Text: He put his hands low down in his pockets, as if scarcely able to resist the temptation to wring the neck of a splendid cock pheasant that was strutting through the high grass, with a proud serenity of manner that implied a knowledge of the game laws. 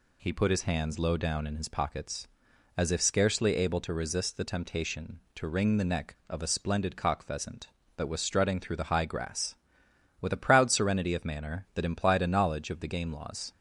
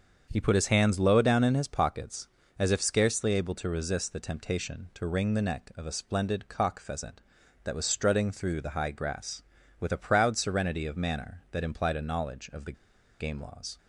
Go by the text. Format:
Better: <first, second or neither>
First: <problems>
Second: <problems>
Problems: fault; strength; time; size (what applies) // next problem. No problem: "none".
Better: first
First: none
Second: starts louder than the rest; until 1.3 s; 7 dB // pauses between "the" and "game"; noticeable; at 12.7 s; 0.47 s long